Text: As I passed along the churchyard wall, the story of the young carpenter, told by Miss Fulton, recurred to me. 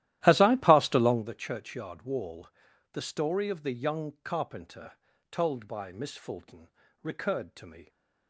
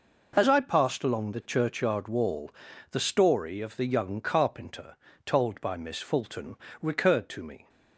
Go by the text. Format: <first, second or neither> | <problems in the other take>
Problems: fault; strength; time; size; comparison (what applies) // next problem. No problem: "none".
second | starts louder than the rest; strong; until 1.2 s; 14 dB